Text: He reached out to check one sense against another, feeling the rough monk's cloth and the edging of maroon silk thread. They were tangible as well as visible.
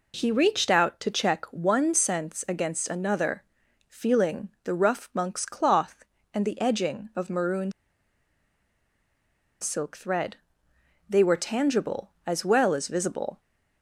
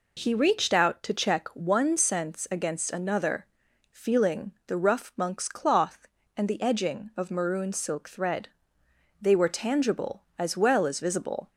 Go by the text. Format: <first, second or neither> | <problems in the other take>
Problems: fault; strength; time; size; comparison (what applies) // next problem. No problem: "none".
second | pauses between "feeling" and "the"; slight; at 4.4 s; 0.16 s long; slight in the second // pauses between "maroon" and "silk"; strong; at 7.7 s; 1.8 s long